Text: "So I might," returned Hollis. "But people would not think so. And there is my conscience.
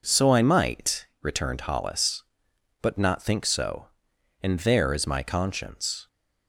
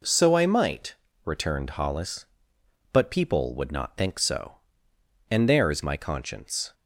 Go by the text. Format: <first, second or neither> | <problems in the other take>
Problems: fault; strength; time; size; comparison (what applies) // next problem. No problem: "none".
second | skips "people would"; at 2.9 s